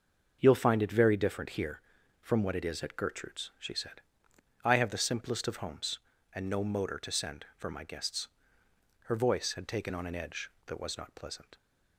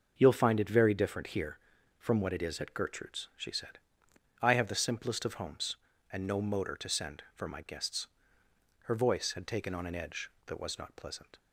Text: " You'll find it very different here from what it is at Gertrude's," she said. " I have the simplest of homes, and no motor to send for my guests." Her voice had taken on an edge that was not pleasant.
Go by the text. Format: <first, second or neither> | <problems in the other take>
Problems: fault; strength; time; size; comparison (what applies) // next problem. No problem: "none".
neither | starts louder than the rest; the same in both